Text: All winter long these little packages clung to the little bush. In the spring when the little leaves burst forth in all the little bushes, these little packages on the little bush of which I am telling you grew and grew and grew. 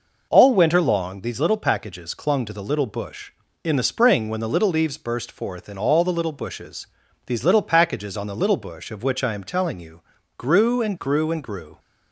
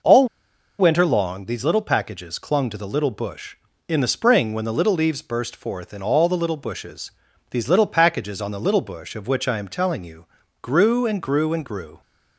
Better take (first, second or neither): first